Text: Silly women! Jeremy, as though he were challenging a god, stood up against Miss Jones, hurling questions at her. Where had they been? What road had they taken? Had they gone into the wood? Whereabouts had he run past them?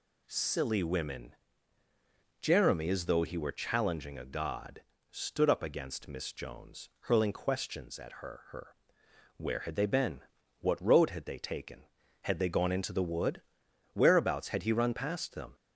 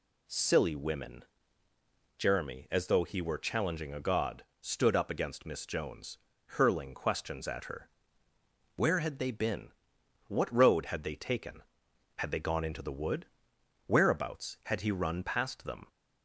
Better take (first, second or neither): second